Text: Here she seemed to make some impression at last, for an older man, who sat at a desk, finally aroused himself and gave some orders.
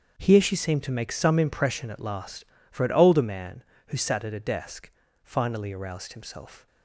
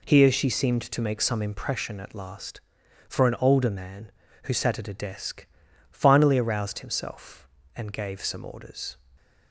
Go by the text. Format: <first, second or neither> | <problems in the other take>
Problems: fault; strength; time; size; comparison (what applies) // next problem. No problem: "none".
second | starts louder than the rest; until 1.2 s; 7 dB // stops before "and gave some orders"; at 6.6 s